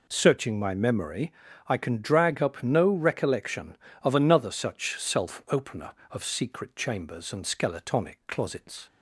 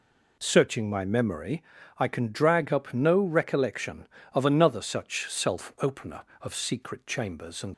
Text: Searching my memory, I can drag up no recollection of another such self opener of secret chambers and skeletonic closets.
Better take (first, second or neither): first